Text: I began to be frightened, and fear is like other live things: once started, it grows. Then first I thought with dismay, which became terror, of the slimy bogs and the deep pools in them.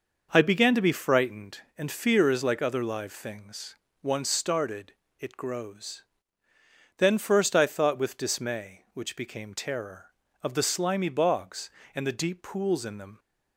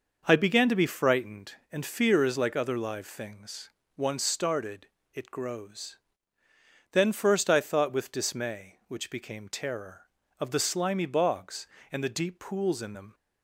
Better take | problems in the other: neither | none

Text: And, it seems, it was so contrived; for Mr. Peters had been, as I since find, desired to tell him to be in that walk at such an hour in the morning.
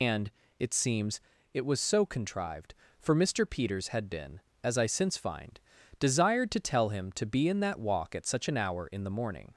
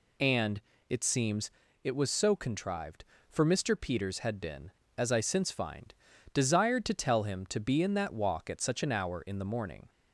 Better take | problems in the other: second | loses the start of "And"; at 0.0 s; 115 ms

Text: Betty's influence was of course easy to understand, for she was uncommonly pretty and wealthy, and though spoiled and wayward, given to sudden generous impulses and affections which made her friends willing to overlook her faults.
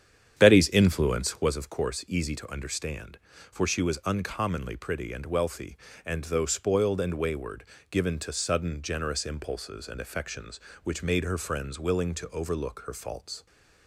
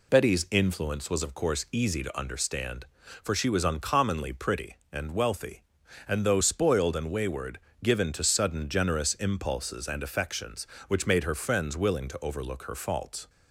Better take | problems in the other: second | starts louder than the rest; strong; until 1.5 s; 8.5 dB

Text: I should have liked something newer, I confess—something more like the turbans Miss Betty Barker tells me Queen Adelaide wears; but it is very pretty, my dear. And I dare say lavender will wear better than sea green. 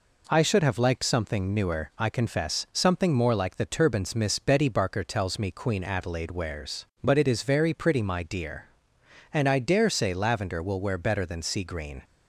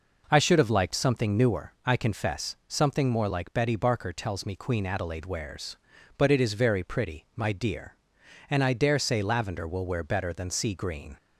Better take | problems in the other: first | skips "the turbans Miss"; at 3.5 s

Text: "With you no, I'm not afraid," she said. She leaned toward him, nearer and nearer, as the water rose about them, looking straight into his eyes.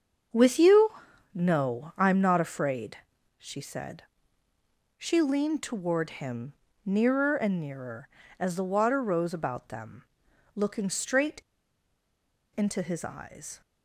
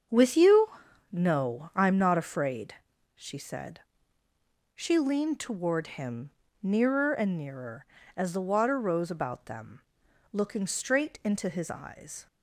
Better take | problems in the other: second | starts louder than the rest; until 1.7 s; 7 dB; also in the second // pauses between "you" and "no"; at 0.9 s; 0.44 s long; also in the second // pauses between "straight" and "into"; at 11.4 s; 1.1 s long

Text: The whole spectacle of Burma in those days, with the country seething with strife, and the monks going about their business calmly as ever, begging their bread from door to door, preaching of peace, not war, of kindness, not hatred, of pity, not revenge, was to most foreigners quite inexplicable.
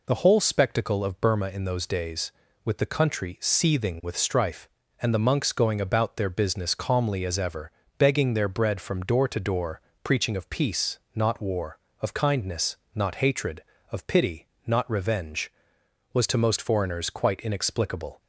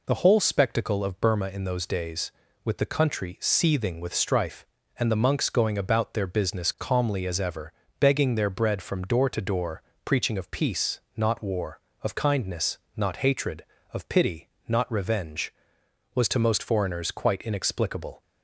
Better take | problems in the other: neither | none

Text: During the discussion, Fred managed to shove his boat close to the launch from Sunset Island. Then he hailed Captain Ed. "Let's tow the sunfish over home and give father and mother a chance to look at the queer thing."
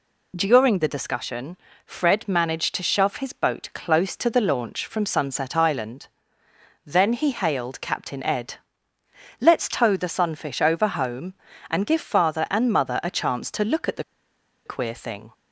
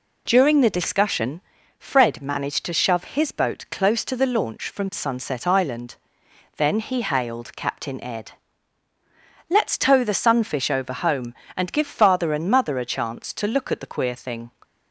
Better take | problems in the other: second | pauses between "the" and "queer"; noticeable; at 14.0 s; 0.62 s long

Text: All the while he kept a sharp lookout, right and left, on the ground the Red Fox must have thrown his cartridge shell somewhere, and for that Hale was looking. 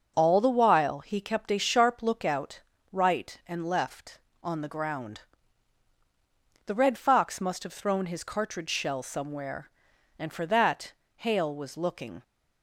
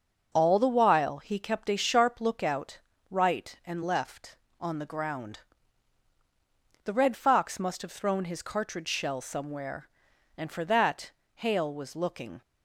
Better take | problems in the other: neither | starts louder than the rest; noticeable; the same in both // pauses between "ground" and "the"; strong; the same in both // pauses between "that" and "Hale"; slight; the same in both

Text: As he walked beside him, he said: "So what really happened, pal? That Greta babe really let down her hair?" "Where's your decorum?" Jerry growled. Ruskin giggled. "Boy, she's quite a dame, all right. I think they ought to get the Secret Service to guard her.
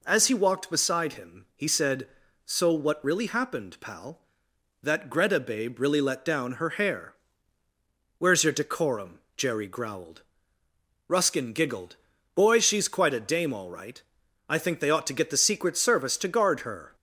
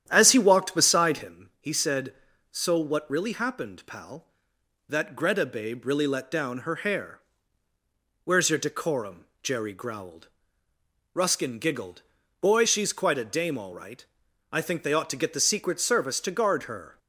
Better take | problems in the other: first | starts louder than the rest; strong; until 1.4 s; 10 dB

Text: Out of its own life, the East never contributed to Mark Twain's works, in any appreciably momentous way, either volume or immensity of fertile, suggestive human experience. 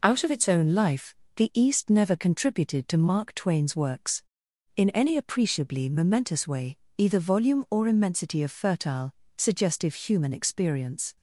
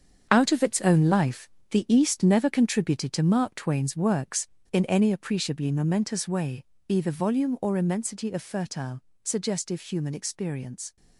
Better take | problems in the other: first | gets quieter; strong; throughout; 10 dB

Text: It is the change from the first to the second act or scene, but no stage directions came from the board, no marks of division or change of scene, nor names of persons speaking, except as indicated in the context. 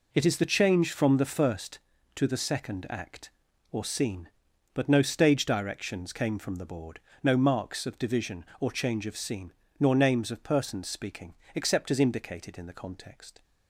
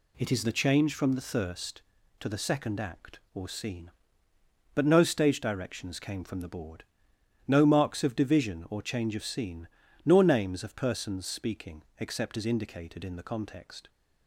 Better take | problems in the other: first | says "thirst" for "first"; at 1.2 s

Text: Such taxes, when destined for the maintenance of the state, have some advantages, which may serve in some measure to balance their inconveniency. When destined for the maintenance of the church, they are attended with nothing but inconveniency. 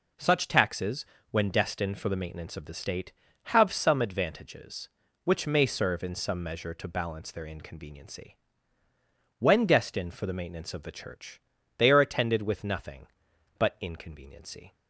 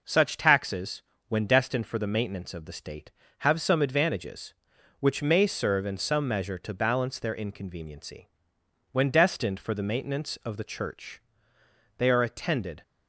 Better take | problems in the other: first | stops before "with nothing but inconveniency"; at 12.8 s

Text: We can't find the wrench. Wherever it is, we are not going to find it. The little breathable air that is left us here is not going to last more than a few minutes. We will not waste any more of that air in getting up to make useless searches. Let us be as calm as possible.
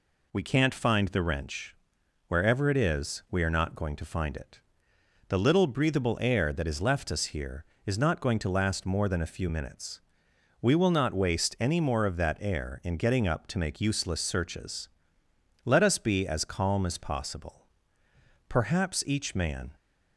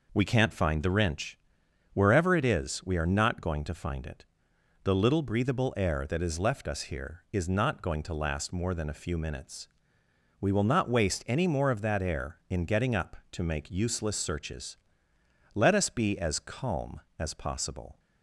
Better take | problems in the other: second | goes on to say "Perhaps each man"; noticeable; from 18.4 s on; 1.2 s long

